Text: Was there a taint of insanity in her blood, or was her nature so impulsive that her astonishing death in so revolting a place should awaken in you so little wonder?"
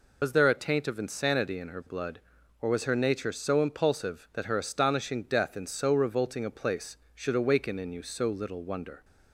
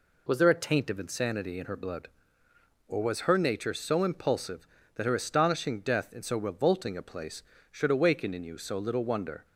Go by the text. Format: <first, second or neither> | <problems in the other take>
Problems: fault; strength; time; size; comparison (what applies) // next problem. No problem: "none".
second | loses the start of "Was"; at 0.2 s; 90 ms